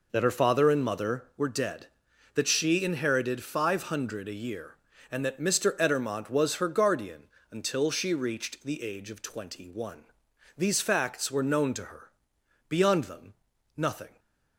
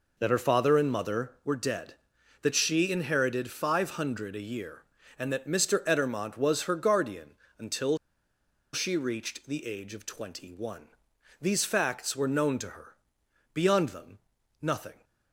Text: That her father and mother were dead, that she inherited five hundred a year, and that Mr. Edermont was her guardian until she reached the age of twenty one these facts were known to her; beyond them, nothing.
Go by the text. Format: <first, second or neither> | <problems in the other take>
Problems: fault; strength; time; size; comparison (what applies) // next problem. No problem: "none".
first | pauses between "guardian" and "until"; slight; at 7.3 s; 0.22 s long; slight in the first // pauses between "until" and "she"; noticeable; at 7.9 s; 0.76 s long // pauses between "one" and "these"; noticeable; at 10.8 s; 0.56 s long; noticeable in the first